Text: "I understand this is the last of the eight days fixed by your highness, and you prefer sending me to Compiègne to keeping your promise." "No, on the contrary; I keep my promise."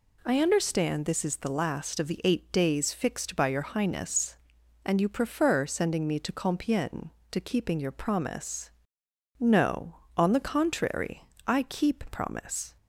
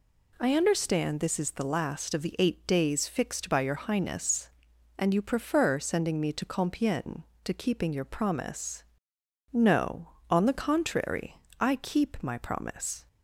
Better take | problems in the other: second | skips "my"; at 12.0 s

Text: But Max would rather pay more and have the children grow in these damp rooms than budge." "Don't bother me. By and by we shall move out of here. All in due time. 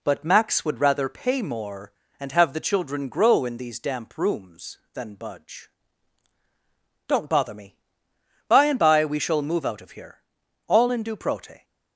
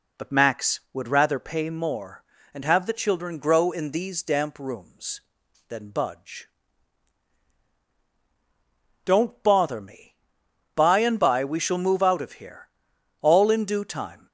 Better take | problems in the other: second | says "prote" for "time"; at 11.1 s

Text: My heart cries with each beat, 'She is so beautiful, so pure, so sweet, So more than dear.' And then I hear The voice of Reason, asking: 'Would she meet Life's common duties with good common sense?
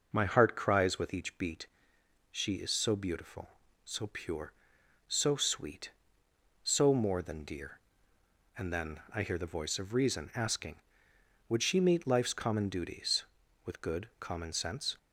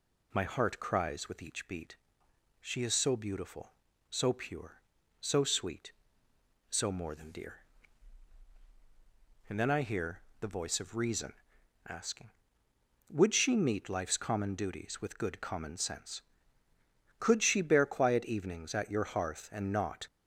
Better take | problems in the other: first | pauses between "hear" and "The"; slight; at 10.2 s; 0.18 s long // goes on to say "Could she bear quiet evenings at your hearth And not"; strong; from 17.1 s on; 2.8 s long

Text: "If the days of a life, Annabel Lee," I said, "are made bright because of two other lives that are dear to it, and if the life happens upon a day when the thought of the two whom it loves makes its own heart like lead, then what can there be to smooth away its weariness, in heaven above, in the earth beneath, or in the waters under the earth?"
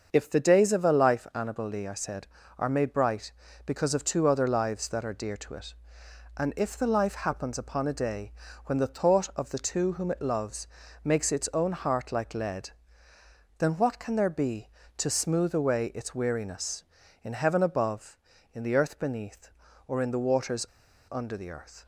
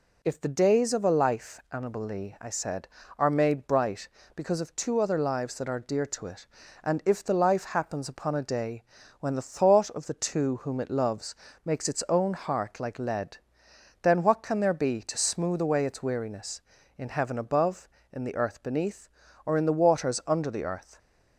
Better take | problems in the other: second | starts louder than the rest; until 1.1 s; 6.5 dB // pauses between "day" and "when"; slight; at 8.3 s; 0.34 s long; also in the second // pauses between "loves" and "makes"; at 10.6 s; 0.38 s long; slight in the second // pauses between "waters" and "under"; at 20.6 s; 0.45 s long

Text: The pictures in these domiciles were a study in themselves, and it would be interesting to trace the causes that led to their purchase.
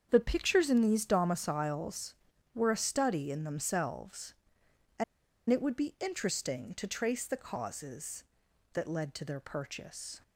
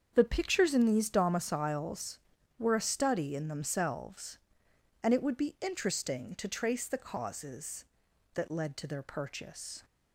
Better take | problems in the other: second | starts louder than the rest; strong; until 1.1 s; 7.5 dB; also in the second // pauses between "and" and "it"; noticeable; at 5.0 s; 0.46 s long

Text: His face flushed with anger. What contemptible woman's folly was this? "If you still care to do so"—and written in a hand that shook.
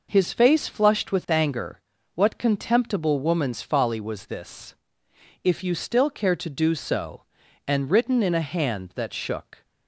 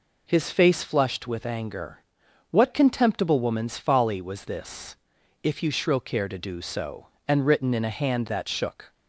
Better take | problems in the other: first | says "shrill" for "still"; at 5.6 s

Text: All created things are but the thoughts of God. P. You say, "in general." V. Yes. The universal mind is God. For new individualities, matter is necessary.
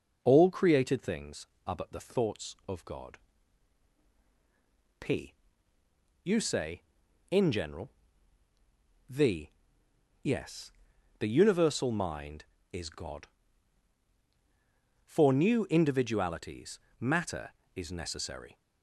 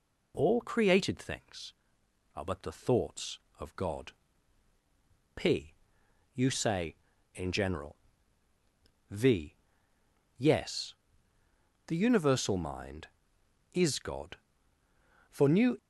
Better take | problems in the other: first | stops before "individualities matter is necessary"; at 15.7 s

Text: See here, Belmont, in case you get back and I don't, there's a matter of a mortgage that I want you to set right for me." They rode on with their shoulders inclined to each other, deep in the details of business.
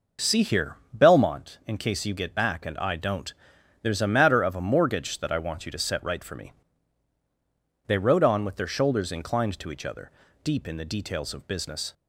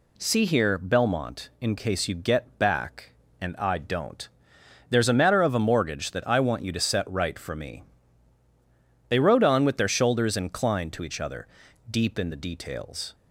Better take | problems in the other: first | stops before "of business"; at 13.1 s

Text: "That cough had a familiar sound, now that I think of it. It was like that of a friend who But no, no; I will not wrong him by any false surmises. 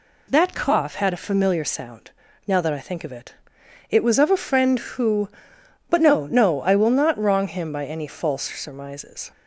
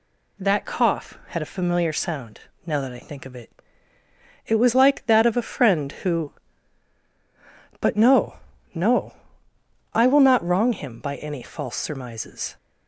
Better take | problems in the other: second | skips "like that"; at 4.1 s

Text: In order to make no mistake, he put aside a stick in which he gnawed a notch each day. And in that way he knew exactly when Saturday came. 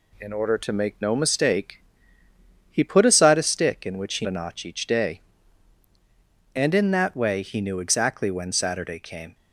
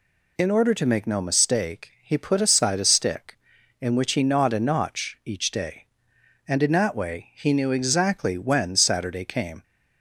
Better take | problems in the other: second | skips "gnawed"; at 4.2 s

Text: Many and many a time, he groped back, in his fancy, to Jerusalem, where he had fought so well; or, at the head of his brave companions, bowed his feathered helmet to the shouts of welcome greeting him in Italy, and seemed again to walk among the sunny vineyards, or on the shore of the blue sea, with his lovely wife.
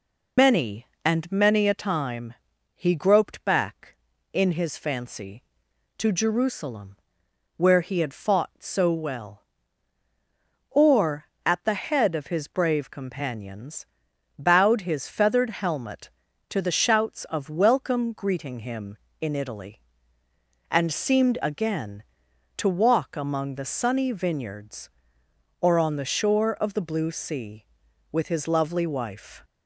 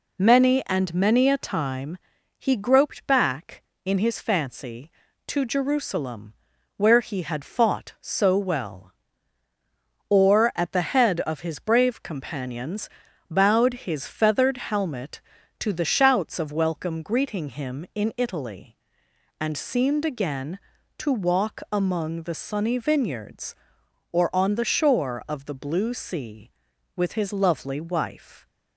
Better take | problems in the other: second | loses the start of "Many"; at 0.3 s; 115 ms

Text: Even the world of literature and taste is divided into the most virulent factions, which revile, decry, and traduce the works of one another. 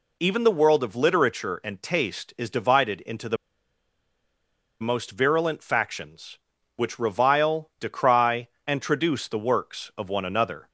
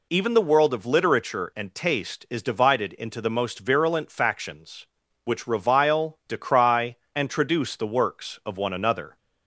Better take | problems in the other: second | pauses between "the" and "most"; strong; at 3.3 s; 1.4 s long

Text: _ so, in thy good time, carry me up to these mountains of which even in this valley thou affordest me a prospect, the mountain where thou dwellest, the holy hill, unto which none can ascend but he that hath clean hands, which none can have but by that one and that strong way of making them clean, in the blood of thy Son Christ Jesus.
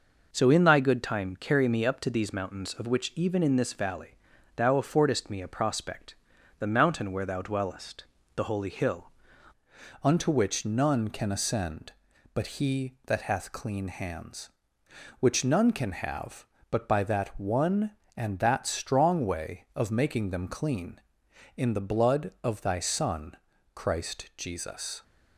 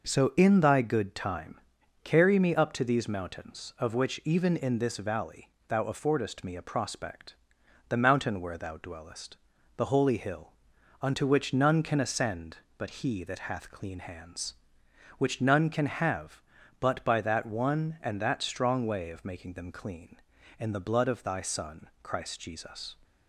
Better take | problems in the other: second | pauses between "valley" and "thou"; at 4.1 s; 0.40 s long; slight in the second // changes voice at "unto"; from 10.0 s on; 15.0 s long // pauses between "Son" and "Christ"; at 23.3 s; 0.40 s long

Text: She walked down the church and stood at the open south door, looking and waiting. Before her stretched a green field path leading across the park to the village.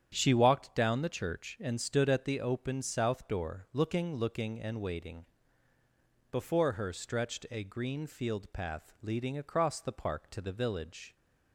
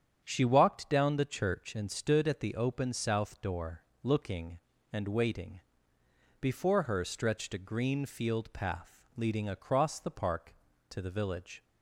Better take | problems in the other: second | starts louder than the rest; strong; until 1.1 s; 9 dB; strong in the second // says "looking" twice; at 4.1 s

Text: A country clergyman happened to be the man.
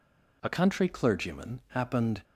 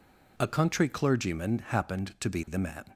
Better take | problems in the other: second | stops before "to be the man"; at 2.2 s

